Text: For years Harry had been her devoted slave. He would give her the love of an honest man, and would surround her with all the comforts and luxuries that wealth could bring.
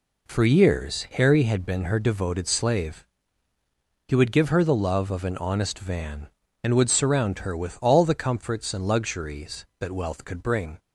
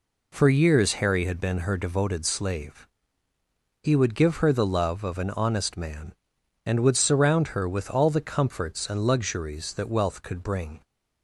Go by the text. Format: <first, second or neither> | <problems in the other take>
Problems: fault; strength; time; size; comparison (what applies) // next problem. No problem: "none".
second | says "van" for "man"; at 5.7 s